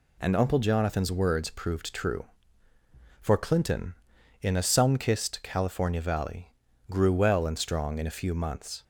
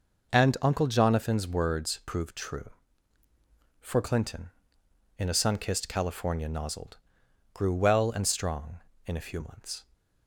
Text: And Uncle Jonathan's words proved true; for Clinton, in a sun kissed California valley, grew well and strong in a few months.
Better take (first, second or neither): first